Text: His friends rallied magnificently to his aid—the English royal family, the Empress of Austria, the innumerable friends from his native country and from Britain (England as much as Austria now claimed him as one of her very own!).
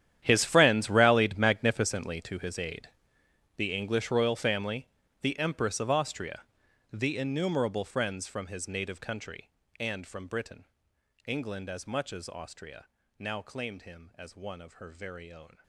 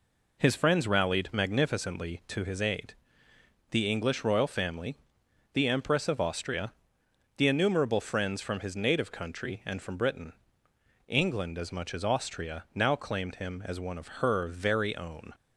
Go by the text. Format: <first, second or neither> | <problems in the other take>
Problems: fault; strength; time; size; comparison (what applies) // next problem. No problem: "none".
second | gets quieter; strong; throughout; 17.5 dB // pauses between "Austria" and "now"; slight; at 12.8 s; 0.34 s long